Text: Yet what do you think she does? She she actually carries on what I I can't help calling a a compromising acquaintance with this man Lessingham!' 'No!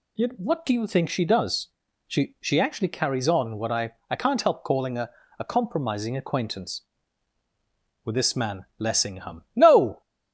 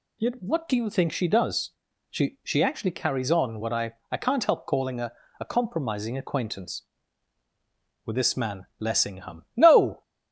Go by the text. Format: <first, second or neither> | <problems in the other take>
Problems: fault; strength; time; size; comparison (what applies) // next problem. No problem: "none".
neither | pauses between "I" and "I"; slight; the same in both // pauses between "a" and "a"; slight; the same in both